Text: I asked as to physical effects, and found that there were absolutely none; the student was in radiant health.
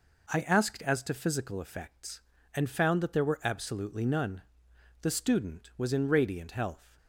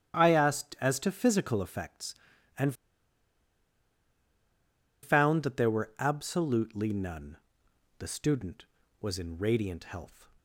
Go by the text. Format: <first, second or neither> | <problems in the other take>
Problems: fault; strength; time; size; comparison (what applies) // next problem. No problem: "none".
first | starts louder than the rest; strong; until 1.2 s; 9.5 dB // pauses between "and" and "found"; strong; at 2.7 s; 2.2 s long